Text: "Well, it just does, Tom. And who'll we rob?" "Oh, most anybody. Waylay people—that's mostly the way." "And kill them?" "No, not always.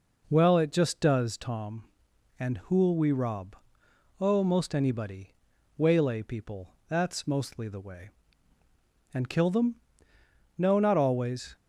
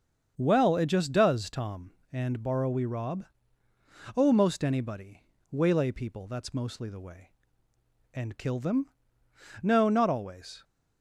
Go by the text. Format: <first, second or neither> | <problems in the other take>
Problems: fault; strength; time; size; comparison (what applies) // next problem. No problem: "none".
first | starts louder than the rest; until 1.3 s; 7 dB // says "borrow" for "who'll"; at 2.4 s